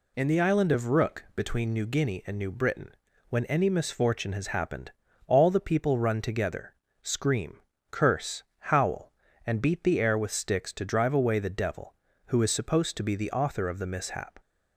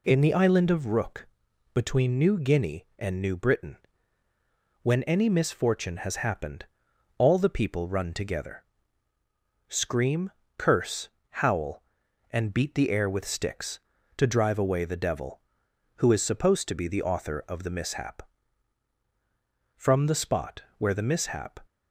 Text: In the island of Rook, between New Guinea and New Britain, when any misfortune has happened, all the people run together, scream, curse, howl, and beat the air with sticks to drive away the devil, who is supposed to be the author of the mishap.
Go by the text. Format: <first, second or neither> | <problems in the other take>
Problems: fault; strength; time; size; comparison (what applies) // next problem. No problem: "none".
first | goes on to say "From the spot where the mishap"; strong; from 19.7 s on; 1.8 s long